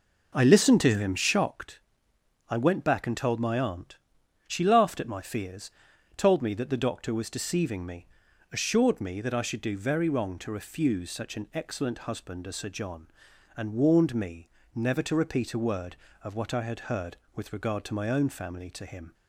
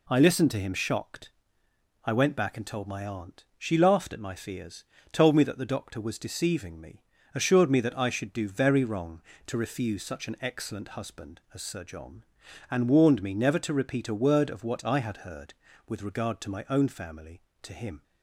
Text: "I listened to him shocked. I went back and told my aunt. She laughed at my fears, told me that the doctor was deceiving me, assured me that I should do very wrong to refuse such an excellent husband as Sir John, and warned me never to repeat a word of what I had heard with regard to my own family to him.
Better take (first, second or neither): second